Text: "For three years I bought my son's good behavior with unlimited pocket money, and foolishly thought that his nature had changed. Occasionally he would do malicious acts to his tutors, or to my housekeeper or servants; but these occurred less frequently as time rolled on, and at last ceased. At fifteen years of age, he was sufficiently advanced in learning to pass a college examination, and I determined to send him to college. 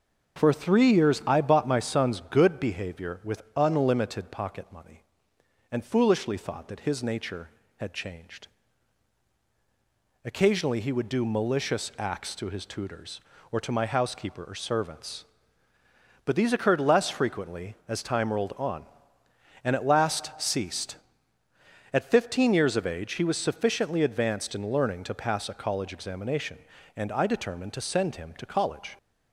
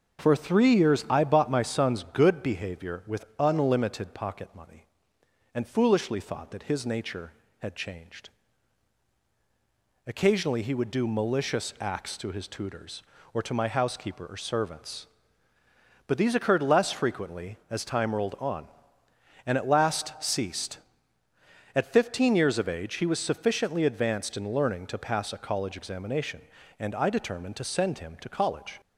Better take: neither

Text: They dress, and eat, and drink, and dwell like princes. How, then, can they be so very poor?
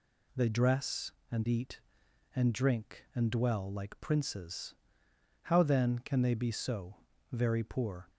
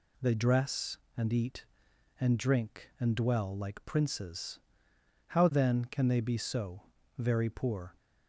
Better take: neither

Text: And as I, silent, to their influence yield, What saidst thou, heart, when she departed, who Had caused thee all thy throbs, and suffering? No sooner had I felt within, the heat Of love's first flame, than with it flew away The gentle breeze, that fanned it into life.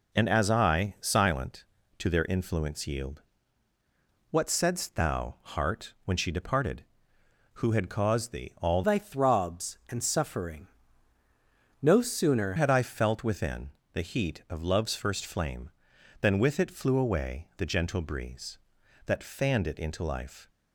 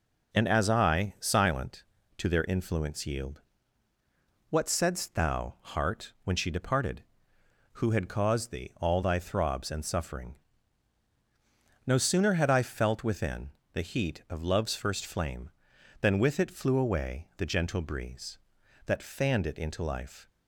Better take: second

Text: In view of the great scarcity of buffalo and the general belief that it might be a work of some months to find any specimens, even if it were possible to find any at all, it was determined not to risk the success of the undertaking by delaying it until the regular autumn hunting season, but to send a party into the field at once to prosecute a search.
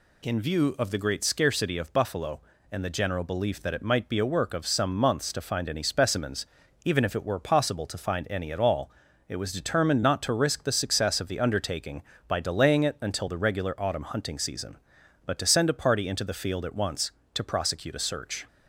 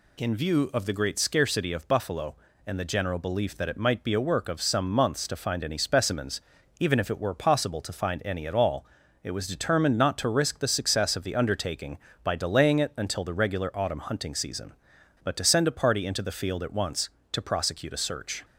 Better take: neither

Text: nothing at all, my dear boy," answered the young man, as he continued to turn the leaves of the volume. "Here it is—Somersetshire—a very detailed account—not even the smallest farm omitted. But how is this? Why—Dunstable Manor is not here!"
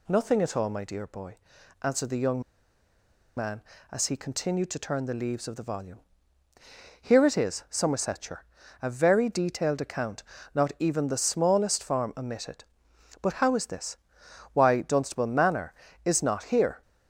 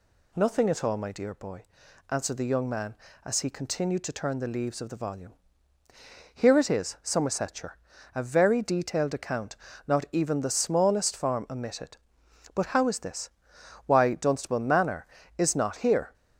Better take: second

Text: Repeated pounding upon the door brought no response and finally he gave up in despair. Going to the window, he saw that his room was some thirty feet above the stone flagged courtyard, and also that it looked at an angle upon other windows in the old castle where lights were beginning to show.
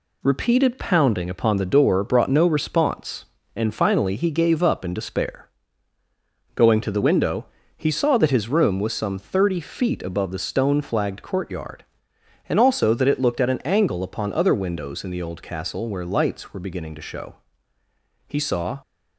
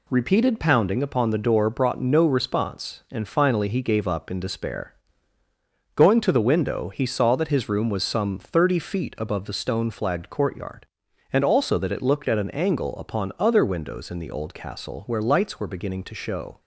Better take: second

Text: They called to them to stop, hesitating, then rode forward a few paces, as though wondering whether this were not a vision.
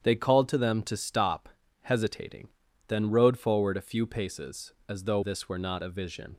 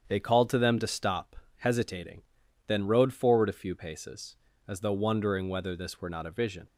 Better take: second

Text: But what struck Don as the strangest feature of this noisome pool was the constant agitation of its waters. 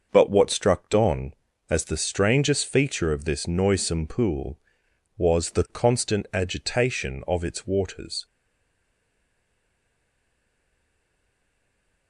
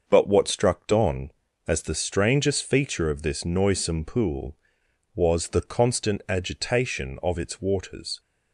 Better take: second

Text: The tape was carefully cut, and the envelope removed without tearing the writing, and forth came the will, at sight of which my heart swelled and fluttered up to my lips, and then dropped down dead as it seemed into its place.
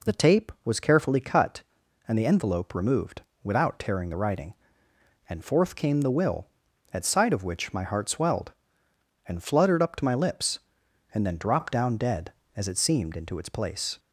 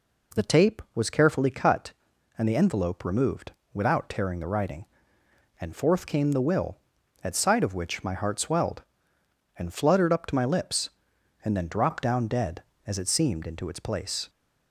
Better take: neither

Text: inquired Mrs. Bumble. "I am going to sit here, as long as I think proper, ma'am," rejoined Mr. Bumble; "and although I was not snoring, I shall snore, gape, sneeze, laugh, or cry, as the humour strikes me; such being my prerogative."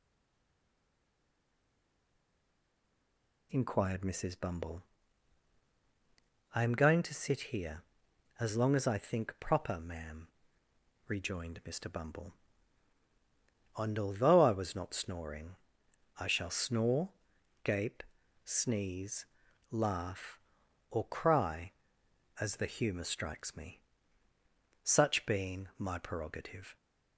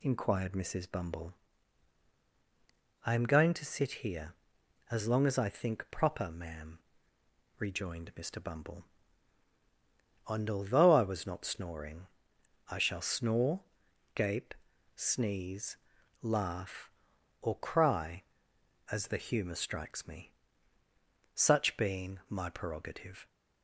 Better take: second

